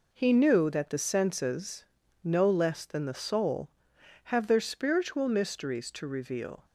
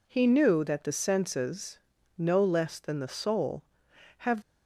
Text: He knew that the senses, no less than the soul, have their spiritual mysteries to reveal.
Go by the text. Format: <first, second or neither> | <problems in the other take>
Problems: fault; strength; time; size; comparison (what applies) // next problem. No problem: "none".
first | stops before "their spiritual mysteries to reveal"; at 4.4 s